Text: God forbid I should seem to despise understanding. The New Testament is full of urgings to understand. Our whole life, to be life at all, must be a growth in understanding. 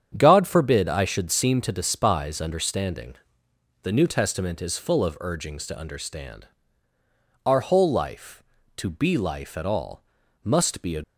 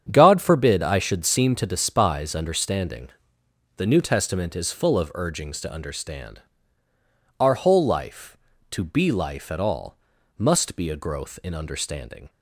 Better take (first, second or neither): second